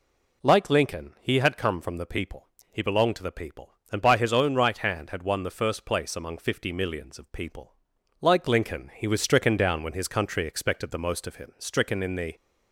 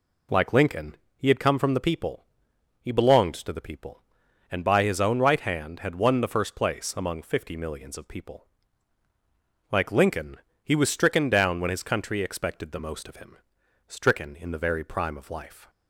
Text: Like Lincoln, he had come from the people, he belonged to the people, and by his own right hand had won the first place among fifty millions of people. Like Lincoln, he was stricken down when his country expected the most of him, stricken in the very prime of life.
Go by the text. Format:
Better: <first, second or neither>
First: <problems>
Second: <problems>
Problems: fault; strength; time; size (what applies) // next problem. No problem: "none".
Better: second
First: stops before "very prime of life"; at 12.3 s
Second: none